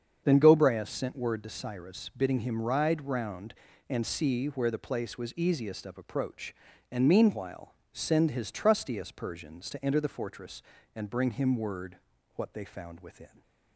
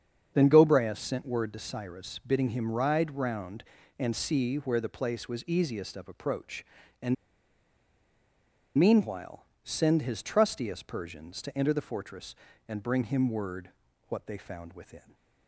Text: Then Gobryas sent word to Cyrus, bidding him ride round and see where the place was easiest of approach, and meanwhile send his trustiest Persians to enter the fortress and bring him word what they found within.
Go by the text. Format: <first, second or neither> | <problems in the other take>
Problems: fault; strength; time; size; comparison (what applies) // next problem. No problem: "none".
first | starts louder than the rest; strong; until 1.3 s; 7.5 dB; strong in the first // pauses between "and" and "meanwhile"; strong; at 7.1 s; 1.6 s long // pauses between "meanwhile" and "send"; slight; at 9.4 s; 0.18 s long; slight in the first // pauses between "word" and "what"; at 13.7 s; 0.38 s long; also in the first